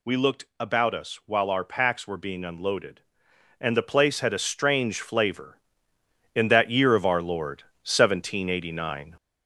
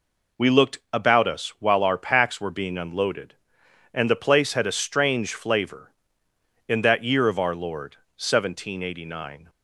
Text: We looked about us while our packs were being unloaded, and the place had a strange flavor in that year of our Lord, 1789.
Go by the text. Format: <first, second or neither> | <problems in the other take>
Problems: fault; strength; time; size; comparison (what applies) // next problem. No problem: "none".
second | gets louder; noticeable; throughout; 4 dB